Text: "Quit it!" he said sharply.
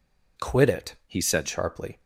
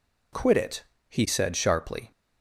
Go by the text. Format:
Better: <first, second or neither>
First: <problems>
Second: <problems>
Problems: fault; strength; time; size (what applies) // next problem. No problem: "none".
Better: second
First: changes voice from "he" to "said"; from 1.0 to 1.4 s; 0.4 s long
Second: none